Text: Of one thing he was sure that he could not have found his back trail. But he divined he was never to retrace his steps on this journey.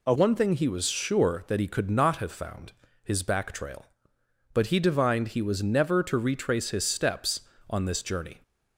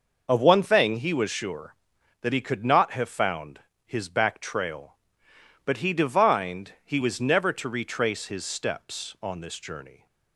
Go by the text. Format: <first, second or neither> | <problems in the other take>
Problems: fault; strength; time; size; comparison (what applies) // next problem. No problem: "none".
second | changes voice at "one"; from 0.1 s on; 8.3 s long // pauses between "found" and "his"; slight; at 2.7 s; 0.32 s long; slight in the second